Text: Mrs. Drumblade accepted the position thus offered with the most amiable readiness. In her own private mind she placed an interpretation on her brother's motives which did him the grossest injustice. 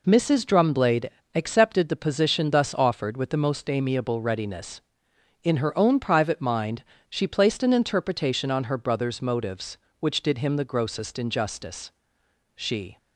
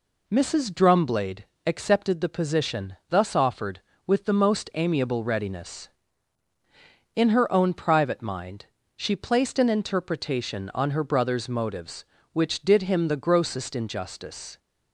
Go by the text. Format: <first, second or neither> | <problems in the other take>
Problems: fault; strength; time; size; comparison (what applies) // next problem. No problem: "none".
second | pauses between "Drumblade" and "accepted"; slight; at 1.0 s; 0.24 s long; slight in the second // pauses between "mind" and "she"; slight; at 6.8 s; 0.26 s long; slight in the second // goes on to say "She"; slight; from 12.5 s on; 0.42 s long